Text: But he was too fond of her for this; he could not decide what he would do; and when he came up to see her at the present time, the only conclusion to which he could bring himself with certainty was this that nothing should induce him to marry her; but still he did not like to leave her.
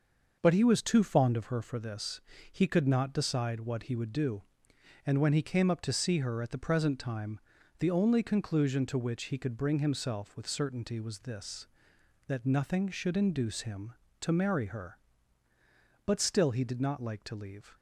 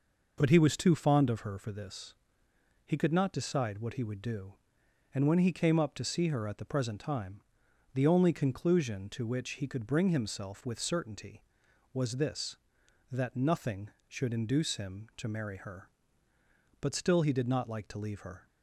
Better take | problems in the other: second | starts louder than the rest; until 1.4 s; 6 dB // stops before "her"; at 17.7 s

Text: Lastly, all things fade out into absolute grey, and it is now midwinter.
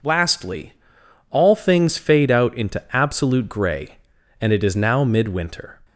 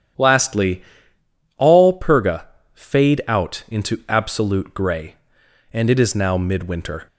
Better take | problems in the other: first | starts louder than the rest; strong; until 1.9 s; 10 dB // says "purga" for "things"; at 1.9 s

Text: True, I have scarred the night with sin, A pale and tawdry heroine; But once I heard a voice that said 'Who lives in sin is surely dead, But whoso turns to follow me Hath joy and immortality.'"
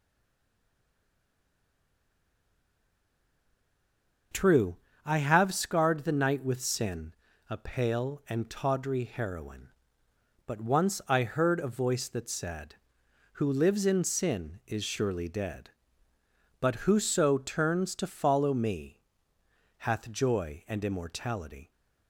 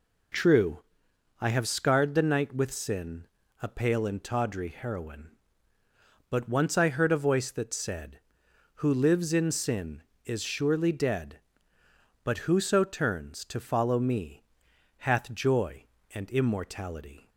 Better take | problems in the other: second | stays silent before the first word; strong; until 4.3 s; 4.3 s long // starts louder than the rest; until 5.6 s; 6 dB // pauses between "me" and "Hath"; noticeable; at 19.0 s; 0.78 s long; noticeable in the second

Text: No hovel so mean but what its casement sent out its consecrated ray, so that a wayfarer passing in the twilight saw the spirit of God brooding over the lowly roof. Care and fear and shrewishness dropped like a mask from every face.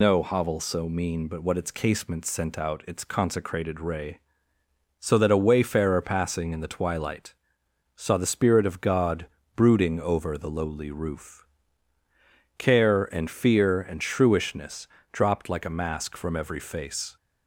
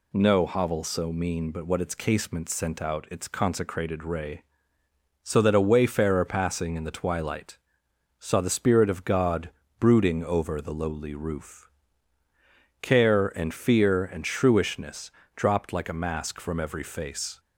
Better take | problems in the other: second | loses the start of "No"; at 0.0 s; 105 ms // pauses between "twilight" and "saw"; noticeable; at 7.3 s; 0.60 s long; noticeable in the second // pauses between "God" and "brooding"; slight; at 9.2 s; 0.30 s long; slight in the second // pauses between "shrewishness" and "dropped"; slight; at 14.8 s; 0.24 s long; slight in the second

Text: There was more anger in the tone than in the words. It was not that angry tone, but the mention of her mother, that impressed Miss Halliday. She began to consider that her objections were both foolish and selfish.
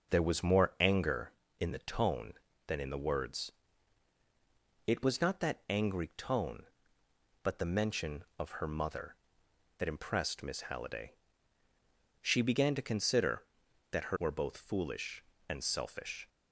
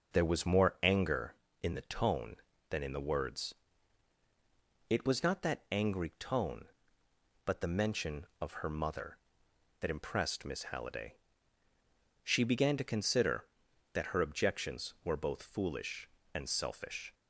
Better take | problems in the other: second | skips "objections"; at 14.1 s

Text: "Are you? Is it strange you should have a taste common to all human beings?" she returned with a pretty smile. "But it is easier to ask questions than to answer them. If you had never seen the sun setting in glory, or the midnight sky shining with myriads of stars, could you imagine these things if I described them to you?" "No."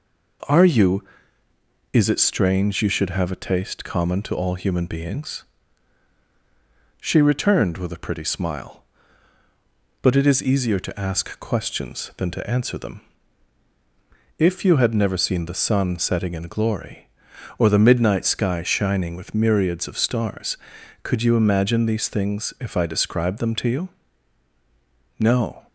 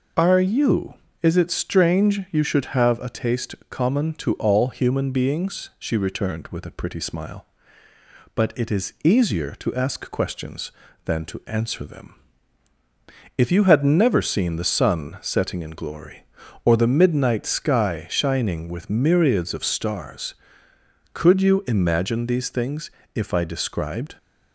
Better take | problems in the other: first | pauses between "taste" and "common"; slight; at 3.5 s; 0.16 s long // pauses between "things" and "if"; slight; at 22.9 s; 0.24 s long // stops before "them to you No"; at 24.1 s

